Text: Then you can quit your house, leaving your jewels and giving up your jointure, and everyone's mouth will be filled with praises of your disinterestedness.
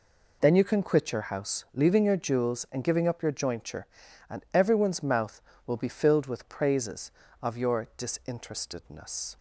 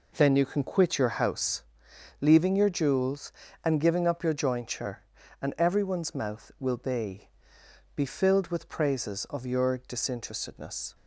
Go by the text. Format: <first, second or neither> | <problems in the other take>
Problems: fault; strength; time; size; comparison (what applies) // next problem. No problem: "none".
first | says "be" twice; at 7.9 s